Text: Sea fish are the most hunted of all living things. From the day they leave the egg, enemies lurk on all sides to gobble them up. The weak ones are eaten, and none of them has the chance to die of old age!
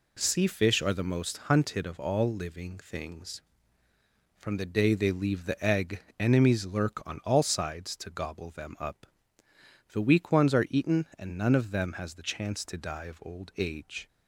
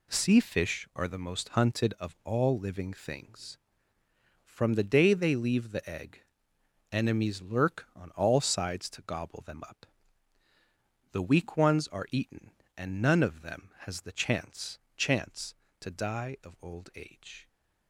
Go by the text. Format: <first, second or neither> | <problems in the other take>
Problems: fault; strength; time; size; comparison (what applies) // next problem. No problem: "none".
first | says "chance" twice; at 14.9 s